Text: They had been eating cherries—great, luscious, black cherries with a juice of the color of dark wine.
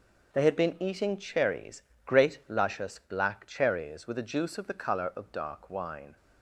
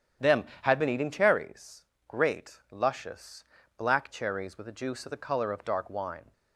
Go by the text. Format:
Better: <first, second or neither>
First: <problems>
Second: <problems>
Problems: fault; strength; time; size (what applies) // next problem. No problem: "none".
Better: first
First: none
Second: starts louder than the rest; strong; until 1.3 s; 9.5 dB // says "Them" for "They"; at 0.2 s